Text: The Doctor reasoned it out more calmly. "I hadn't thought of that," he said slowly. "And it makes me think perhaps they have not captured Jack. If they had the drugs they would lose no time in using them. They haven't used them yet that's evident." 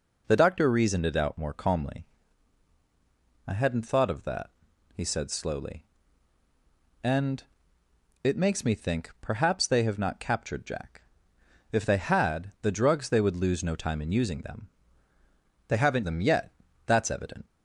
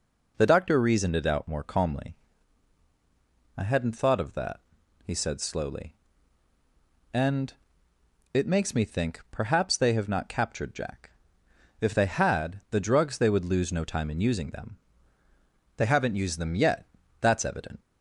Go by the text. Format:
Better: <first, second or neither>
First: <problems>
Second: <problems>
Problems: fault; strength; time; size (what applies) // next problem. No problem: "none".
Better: second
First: pauses between "And" and "it"; noticeable; at 7.4 s; 0.80 s long // skips "used"; at 16.0 s // pauses between "yet" and "that's"; slight; at 16.5 s; 0.32 s long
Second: pauses between "And" and "it"; noticeable; at 7.5 s; 0.80 s long // pauses between "yet" and "that's"; slight; at 16.8 s; 0.32 s long